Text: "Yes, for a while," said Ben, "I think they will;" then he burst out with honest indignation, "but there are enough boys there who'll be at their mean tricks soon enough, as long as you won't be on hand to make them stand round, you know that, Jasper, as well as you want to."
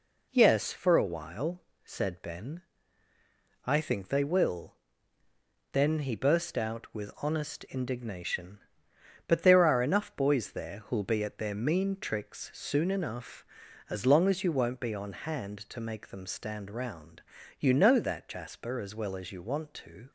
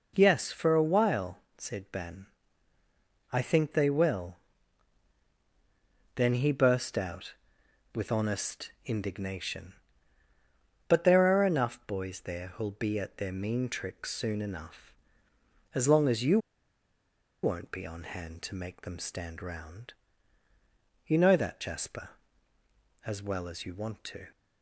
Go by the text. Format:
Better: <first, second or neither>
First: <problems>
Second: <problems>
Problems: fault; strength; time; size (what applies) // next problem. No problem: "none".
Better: first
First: none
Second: pauses between "you" and "won't"; at 16.3 s; 1.0 s long